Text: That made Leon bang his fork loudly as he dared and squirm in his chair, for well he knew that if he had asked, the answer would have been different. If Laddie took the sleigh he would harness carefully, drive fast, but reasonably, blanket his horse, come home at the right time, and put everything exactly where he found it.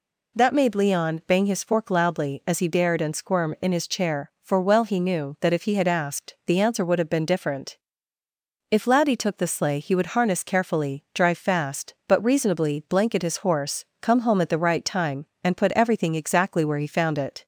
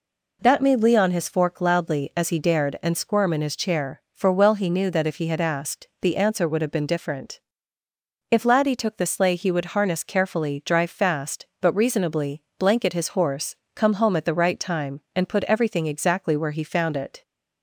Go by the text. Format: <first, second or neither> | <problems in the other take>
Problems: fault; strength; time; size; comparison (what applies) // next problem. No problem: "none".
first | skips "bang"; at 1.1 s